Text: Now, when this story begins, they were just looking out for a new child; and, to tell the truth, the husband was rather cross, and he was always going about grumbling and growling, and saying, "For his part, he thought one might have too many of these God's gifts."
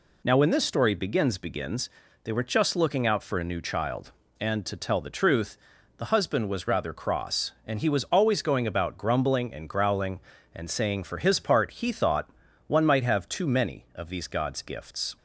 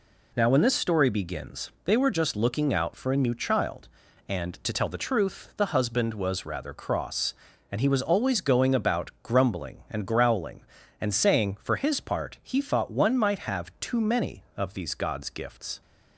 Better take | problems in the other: second | says "begins" twice; at 1.3 s // pauses between "thought" and "one"; at 12.3 s; 0.38 s long

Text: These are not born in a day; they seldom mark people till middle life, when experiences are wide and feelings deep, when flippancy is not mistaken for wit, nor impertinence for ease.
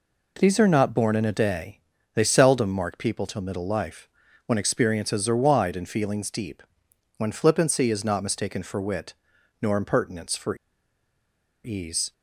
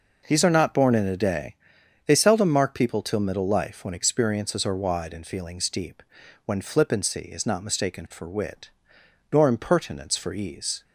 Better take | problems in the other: second | pauses between "for" and "ease"; at 10.5 s; 1.0 s long

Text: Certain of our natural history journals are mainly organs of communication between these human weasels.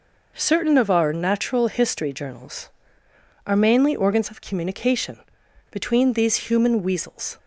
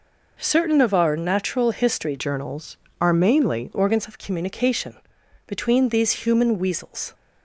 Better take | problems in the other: first | changes voice from "journals" to "mainly"; from 2.1 to 3.6 s; 1.5 s long // pauses between "communication" and "between"; noticeable; at 4.9 s; 0.52 s long; noticeable in the first

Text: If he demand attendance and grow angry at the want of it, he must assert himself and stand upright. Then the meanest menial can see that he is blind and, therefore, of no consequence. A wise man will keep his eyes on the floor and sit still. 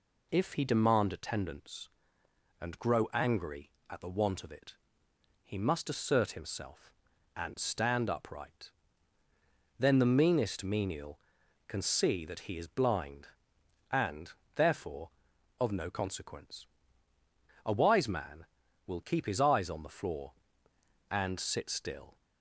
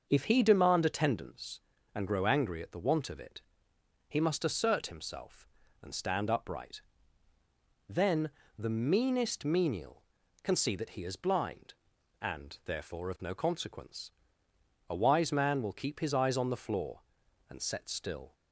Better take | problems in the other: first | starts louder than the rest; until 1.1 s; 6.5 dB // pauses between "Then" and "the"; slight; at 8.2 s; 0.28 s long // says "set" for "sit"; at 17.6 s

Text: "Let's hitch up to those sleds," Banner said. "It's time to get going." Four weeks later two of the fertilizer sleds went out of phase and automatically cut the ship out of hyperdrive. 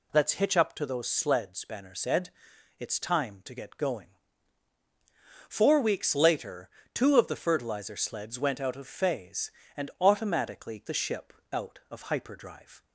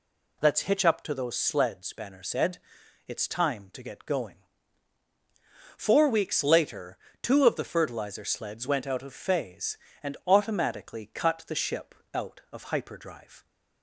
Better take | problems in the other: second | pauses between "later" and "two"; slight; at 6.6 s; 0.26 s long; slight in the second // skips "cut"; at 10.8 s // pauses between "ship" and "out"; slight; at 11.3 s; 0.18 s long; slight in the second

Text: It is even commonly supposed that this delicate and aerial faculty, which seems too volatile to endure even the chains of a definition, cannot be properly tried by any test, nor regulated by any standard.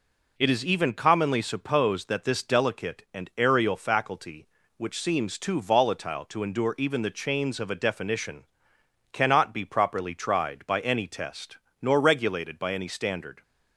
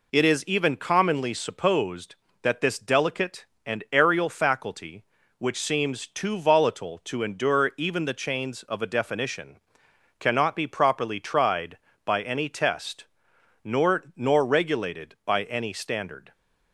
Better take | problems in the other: first | says "nor" twice; at 14.1 s

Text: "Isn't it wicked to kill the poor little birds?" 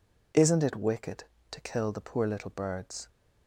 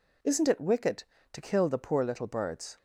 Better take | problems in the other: neither | none

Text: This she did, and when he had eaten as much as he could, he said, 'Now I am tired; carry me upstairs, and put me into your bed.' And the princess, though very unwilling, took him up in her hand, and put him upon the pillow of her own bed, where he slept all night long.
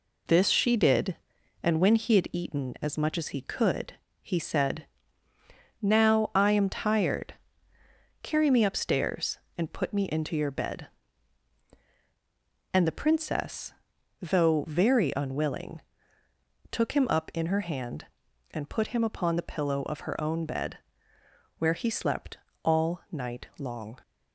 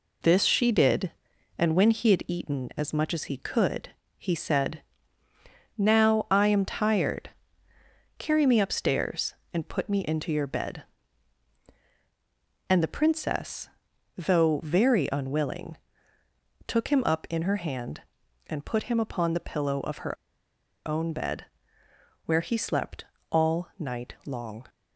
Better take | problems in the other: first | pauses between "her" and "own"; noticeable; at 20.1 s; 0.72 s long // pauses between "slept" and "all"; slight; at 23.0 s; 0.26 s long; slight in the first

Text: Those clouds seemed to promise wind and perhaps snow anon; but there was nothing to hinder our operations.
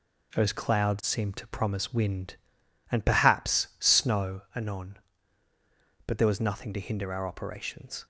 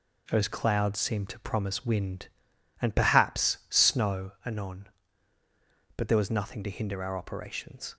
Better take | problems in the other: neither | none

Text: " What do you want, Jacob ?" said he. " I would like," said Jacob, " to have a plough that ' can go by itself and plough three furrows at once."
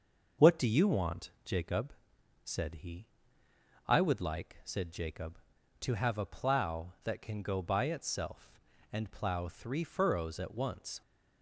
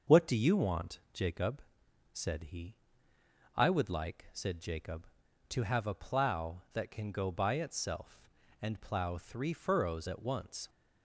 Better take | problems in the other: neither | starts louder than the rest; the same in both

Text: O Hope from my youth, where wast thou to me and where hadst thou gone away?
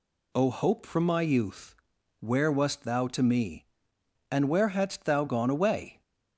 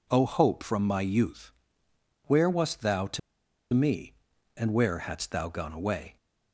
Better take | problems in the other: first | pauses between "to" and "me"; noticeable; at 3.1 s; 0.54 s long

